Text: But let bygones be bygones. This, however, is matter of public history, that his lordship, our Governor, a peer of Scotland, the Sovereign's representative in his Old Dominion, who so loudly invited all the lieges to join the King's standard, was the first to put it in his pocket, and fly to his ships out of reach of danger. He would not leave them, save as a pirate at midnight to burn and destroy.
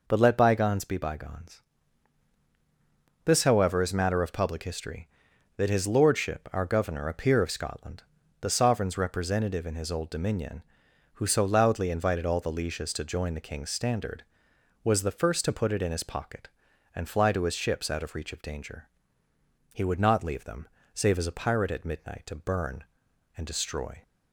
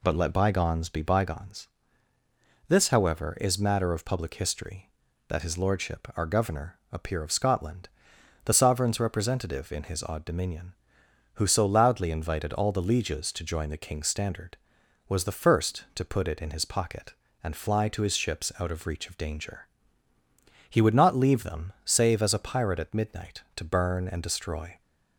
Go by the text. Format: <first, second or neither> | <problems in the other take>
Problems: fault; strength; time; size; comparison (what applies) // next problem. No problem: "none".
first | says "Odd" for "Old"; at 10.0 s